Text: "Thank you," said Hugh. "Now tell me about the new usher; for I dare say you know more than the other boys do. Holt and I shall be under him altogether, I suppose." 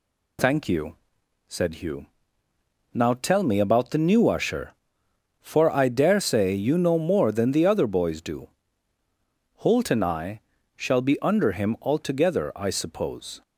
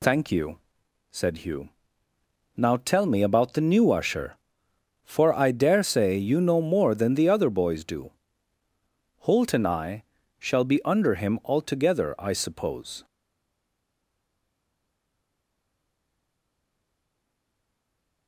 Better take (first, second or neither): first